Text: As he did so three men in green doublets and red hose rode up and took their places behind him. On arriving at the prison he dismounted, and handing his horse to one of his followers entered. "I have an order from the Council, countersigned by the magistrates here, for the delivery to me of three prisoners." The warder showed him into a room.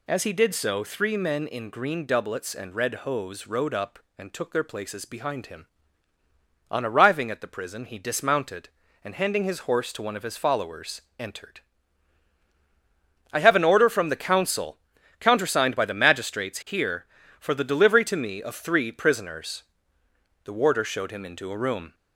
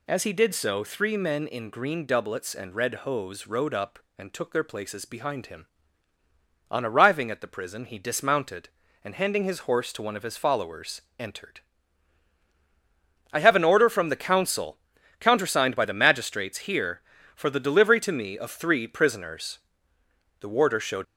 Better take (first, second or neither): first